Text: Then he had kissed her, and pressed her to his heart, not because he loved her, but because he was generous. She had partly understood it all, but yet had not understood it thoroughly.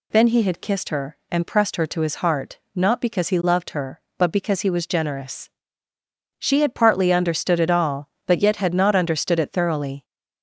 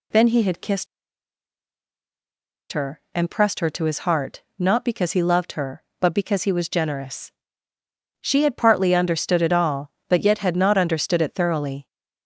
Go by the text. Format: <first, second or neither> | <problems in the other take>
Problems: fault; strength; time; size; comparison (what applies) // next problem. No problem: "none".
first | pauses between "kissed" and "her"; strong; at 0.8 s; 1.8 s long